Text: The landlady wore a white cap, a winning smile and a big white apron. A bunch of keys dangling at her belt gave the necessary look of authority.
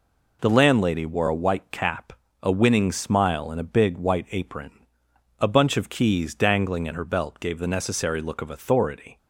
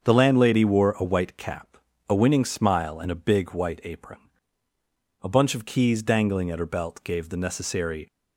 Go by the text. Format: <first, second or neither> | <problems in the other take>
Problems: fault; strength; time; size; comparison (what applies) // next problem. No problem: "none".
first | starts louder than the rest; until 1.0 s; 7 dB // stops before "look of authority"; at 8.1 s